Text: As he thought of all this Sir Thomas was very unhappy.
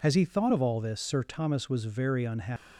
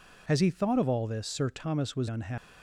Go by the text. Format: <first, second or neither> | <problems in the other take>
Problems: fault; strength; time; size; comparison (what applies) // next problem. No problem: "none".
first | skips "very"; at 2.0 s